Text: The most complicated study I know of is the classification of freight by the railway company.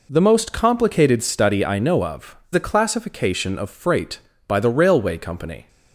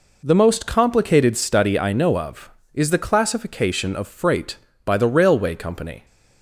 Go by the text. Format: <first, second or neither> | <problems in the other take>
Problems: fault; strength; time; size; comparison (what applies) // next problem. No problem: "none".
second | skips "is"; at 2.4 s